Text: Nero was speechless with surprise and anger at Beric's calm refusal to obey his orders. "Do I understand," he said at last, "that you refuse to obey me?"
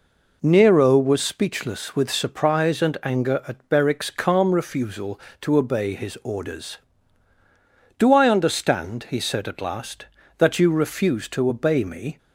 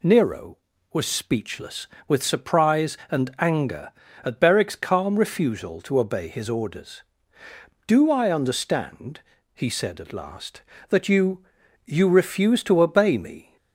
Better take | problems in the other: first | says "you" twice; at 11.8 s

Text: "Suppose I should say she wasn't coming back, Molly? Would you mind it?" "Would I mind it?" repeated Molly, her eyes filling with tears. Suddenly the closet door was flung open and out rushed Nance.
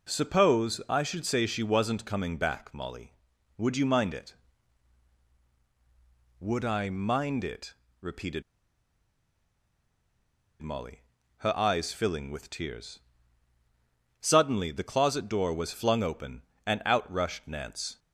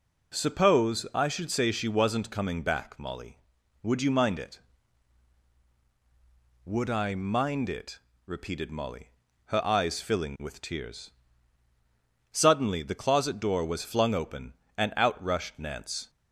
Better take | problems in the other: second | pauses between "repeated" and "Molly"; strong; at 8.4 s; 2.1 s long

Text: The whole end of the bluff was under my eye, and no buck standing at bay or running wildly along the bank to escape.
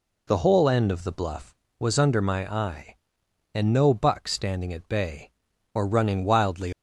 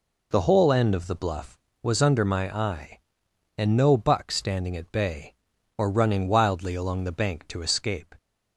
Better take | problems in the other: second | stops before "along the bank to escape"; at 6.7 s

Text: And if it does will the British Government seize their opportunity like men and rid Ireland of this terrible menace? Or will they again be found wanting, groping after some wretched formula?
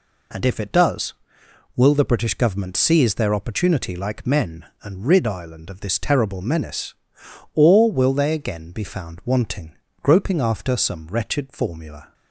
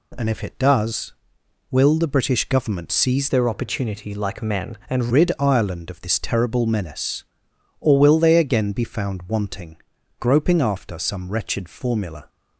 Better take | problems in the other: first | changes voice from "their" to "and"; from 3.2 to 5.1 s; 1.9 s long

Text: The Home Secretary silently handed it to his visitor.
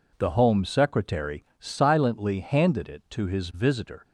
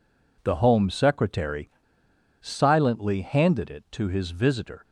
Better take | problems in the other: first | pauses between "Secretary" and "silently"; noticeable; at 1.6 s; 0.70 s long

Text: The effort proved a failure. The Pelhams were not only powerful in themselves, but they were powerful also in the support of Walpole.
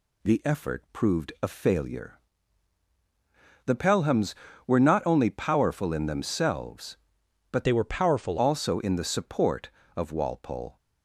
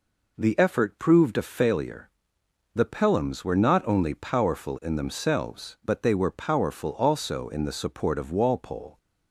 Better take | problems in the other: second | changes voice from "they" to "powerful"; from 7.6 to 8.3 s; 0.7 s long

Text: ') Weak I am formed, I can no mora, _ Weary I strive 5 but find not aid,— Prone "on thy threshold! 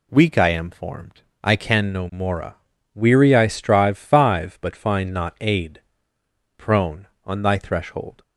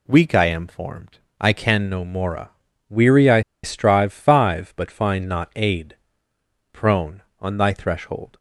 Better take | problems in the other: first | pauses between "I" and "strive"; slight; at 3.4 s; 0.22 s long

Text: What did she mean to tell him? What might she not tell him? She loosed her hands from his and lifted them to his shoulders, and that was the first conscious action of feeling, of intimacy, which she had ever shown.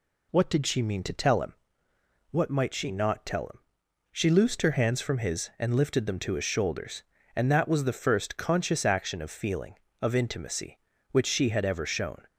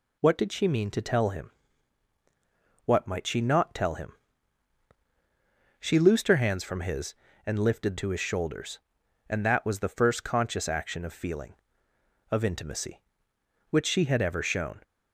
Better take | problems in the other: first | skips "them"; at 7.9 s

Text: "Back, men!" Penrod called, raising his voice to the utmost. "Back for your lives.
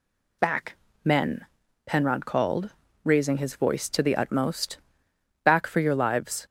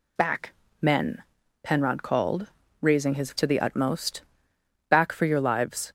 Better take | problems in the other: first | skips "voice"; at 3.3 s

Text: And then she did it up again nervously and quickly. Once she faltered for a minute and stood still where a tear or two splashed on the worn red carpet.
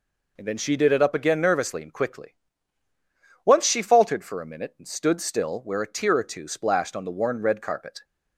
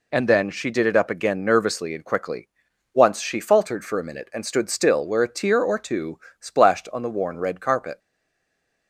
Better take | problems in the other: first | pauses between "two" and "splashed"; slight; at 6.1 s; 0.22 s long // stays silent after the last word; slight; from 7.9 s on; 0.9 s long

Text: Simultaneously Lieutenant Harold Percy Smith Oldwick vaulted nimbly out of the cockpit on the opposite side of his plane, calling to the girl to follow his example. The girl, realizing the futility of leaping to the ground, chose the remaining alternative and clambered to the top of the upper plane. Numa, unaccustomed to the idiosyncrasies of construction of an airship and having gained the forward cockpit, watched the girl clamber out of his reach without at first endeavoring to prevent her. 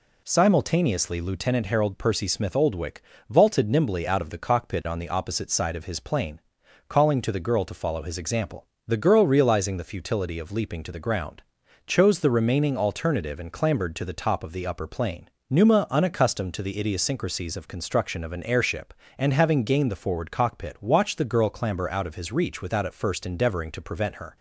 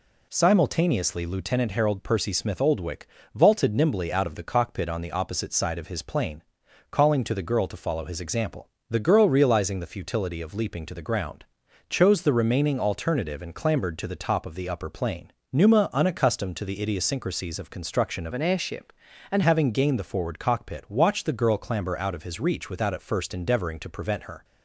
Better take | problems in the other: first | pauses between "Oldwick" and "vaulted"; slight; at 3.0 s; 0.28 s long; slight in the first // changes voice from "an" to "and"; from 18.3 to 19.4 s; 1.1 s long

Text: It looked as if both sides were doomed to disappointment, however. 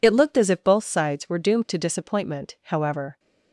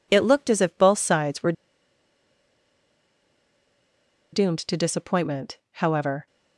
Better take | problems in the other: first | pauses between "were" and "doomed"; strong; at 1.5 s; 2.8 s long

